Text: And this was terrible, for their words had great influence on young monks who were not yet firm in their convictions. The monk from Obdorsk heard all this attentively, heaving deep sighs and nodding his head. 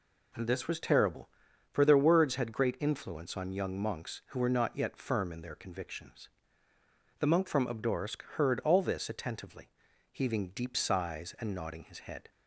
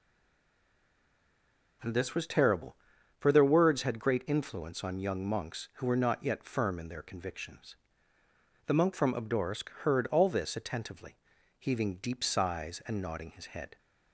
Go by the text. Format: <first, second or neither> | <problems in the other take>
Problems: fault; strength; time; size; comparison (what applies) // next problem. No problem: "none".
first | stays silent before the first word; noticeable; until 1.8 s; 1.8 s long